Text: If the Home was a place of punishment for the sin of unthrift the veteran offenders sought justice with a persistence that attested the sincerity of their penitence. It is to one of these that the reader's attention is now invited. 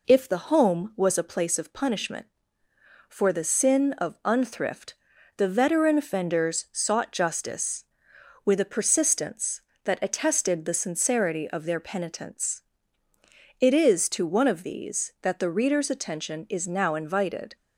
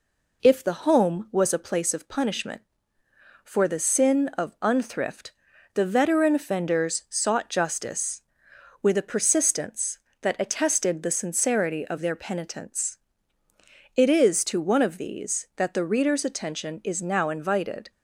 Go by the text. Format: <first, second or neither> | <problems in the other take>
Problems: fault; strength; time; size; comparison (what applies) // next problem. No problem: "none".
neither | pauses between "unthrift" and "the"; the same in both